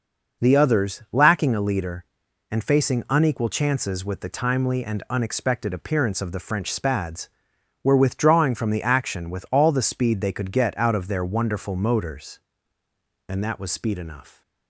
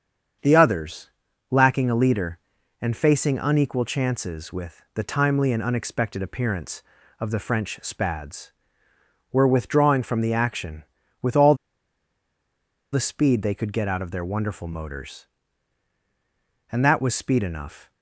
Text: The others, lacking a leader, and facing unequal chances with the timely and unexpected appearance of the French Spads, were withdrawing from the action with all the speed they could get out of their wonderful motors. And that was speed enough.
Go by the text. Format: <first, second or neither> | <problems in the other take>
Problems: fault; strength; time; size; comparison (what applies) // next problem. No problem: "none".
first | starts louder than the rest; strong; until 1.8 s; 7 dB // pauses between "all" and "the"; strong; at 11.5 s; 1.3 s long